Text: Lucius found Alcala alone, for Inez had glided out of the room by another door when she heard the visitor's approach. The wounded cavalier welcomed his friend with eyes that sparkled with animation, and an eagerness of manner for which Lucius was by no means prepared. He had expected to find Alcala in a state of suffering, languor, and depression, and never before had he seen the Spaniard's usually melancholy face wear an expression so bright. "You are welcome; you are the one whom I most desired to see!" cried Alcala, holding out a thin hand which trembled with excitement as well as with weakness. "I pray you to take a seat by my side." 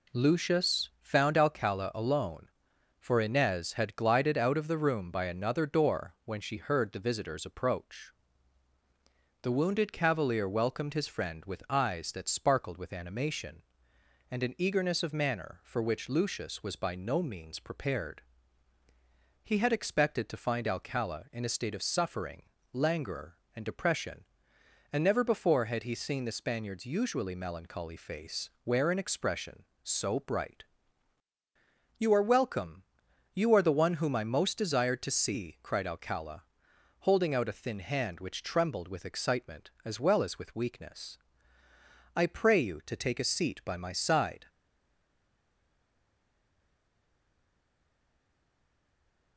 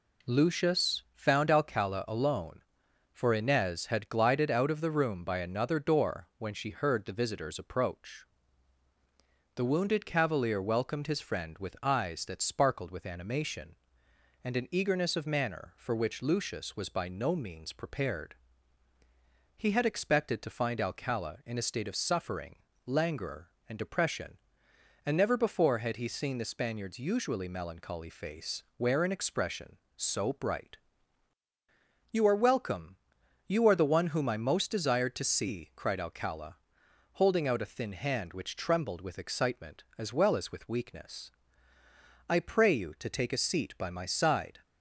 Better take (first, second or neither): second